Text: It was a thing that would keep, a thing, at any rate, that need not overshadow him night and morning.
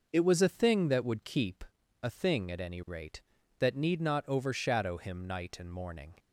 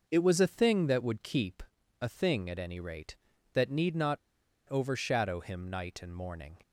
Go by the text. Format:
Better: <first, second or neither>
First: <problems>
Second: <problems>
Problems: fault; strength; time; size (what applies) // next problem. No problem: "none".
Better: first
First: none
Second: pauses between "not" and "overshadow"; noticeable; at 4.1 s; 0.53 s long